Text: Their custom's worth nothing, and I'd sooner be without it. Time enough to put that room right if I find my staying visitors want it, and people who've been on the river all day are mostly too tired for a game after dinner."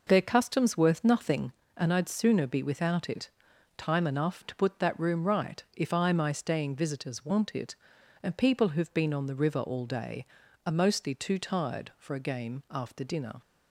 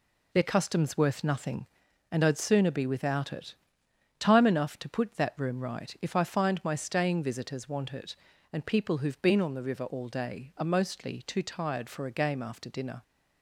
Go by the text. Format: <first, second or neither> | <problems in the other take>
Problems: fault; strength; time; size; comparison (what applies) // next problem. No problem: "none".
second | skips "find"; at 6.1 s